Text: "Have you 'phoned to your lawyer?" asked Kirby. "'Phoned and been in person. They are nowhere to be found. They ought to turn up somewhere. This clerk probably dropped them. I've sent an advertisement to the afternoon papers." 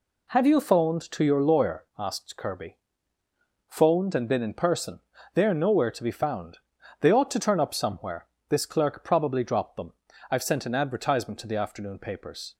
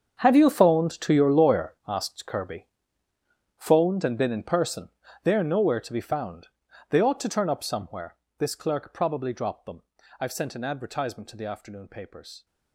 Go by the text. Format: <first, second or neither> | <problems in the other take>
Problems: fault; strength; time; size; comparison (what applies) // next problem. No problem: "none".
first | gets quieter; strong; throughout; 16.5 dB